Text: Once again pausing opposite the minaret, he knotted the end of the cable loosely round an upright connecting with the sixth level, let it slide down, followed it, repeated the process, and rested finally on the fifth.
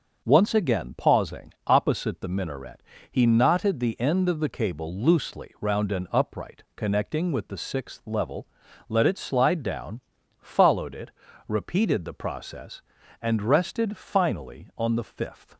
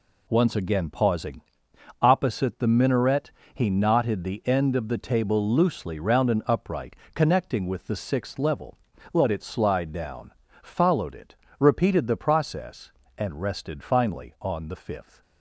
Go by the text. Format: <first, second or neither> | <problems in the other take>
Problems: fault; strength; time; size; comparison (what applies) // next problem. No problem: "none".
first | pauses between "pausing" and "opposite"; noticeable; at 1.4 s; 0.60 s long // says "table" for "cable"; at 4.9 s // pauses between "upright" and "connecting"; slight; at 6.9 s; 0.18 s long